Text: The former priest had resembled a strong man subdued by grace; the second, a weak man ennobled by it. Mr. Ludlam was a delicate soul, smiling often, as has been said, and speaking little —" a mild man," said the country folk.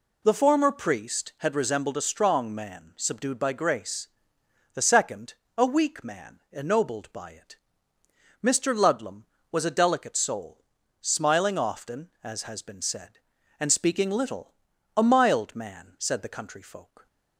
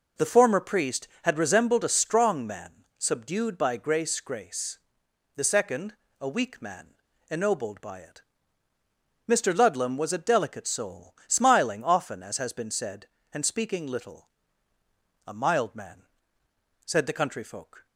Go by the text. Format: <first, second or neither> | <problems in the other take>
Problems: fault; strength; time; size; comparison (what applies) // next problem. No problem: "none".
first | says "grace" twice; at 4.2 s // pauses between "man" and "ennobled"; slight; at 6.9 s; 0.36 s long